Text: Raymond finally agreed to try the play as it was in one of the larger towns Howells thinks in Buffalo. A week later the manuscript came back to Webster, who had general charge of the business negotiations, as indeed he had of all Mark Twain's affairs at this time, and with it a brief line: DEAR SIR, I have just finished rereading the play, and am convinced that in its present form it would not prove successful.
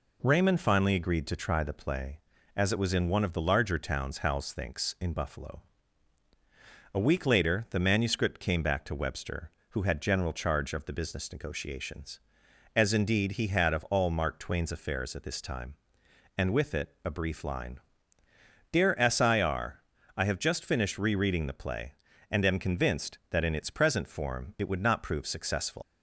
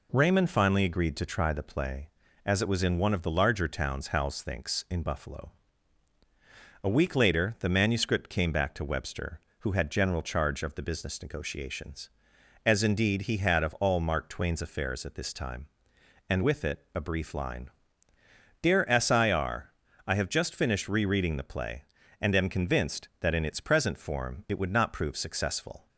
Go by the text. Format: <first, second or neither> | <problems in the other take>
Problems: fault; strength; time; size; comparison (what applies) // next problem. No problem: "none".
second | leaves "successful" unfinished; at 25.8 s; 155 ms